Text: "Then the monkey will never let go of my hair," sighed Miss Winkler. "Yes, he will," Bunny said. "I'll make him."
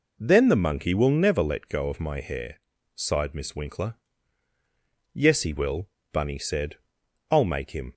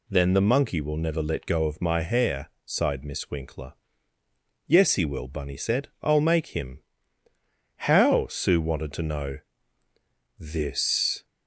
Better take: first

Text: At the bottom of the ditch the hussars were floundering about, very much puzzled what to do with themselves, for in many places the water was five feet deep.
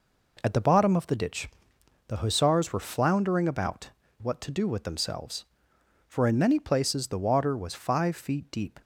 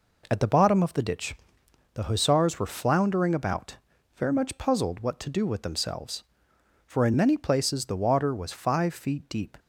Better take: second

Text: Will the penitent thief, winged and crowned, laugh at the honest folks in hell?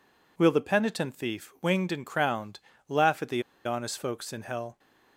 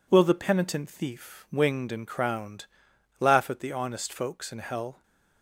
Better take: second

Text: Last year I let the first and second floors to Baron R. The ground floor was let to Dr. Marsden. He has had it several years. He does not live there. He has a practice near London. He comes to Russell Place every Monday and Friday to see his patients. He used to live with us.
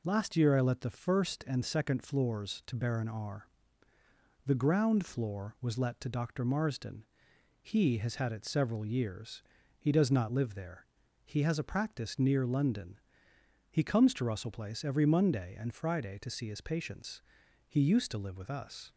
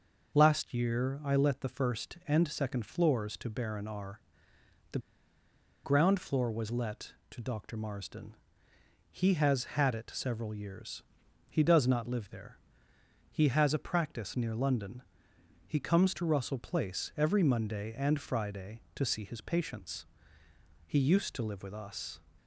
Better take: first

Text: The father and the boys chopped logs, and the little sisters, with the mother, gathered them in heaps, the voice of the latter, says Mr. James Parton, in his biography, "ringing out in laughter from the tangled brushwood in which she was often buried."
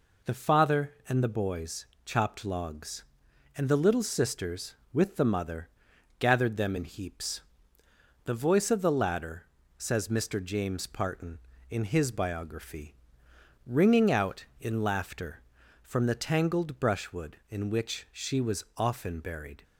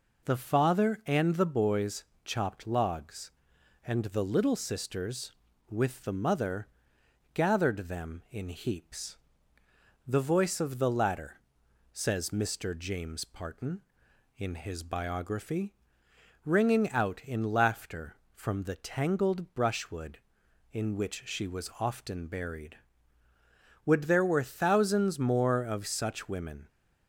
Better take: first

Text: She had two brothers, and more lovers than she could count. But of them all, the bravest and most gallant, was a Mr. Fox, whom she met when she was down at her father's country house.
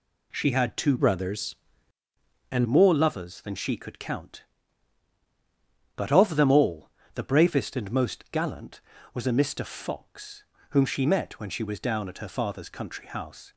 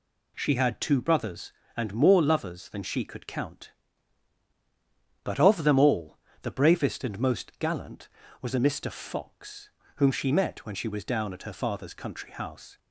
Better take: second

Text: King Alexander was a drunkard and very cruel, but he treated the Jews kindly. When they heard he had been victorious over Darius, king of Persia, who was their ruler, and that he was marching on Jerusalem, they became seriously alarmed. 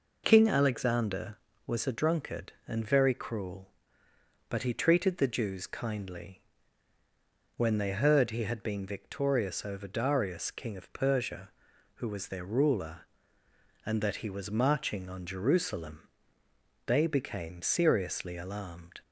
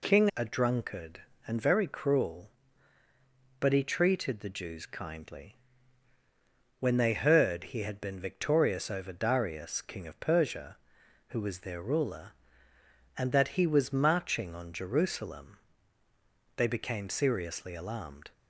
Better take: first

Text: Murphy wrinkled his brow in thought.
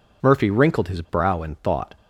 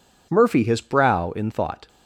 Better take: first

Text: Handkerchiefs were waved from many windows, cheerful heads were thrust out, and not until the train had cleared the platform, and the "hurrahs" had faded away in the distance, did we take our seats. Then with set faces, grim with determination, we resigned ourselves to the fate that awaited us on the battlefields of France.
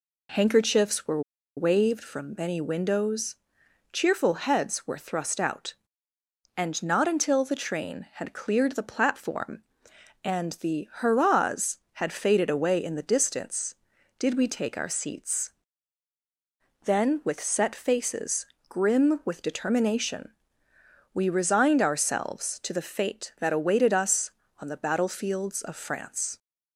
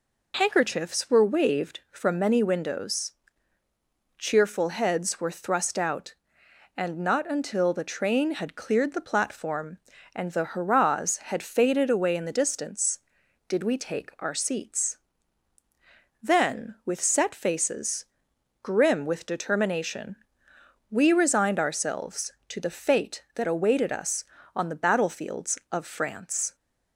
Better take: second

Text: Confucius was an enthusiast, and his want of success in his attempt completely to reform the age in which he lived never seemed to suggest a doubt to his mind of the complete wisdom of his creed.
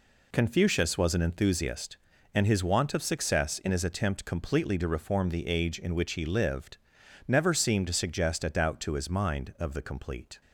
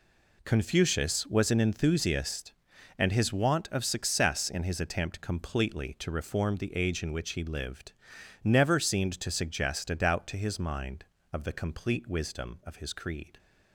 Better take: second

